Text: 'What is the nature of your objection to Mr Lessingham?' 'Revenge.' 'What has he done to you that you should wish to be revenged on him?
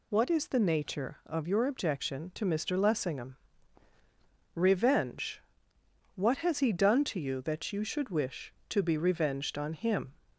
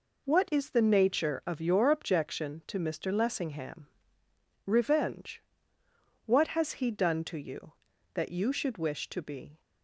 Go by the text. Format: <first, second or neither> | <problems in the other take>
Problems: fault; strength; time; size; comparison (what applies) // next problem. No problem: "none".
first | stops before "revenged on him"; at 9.5 s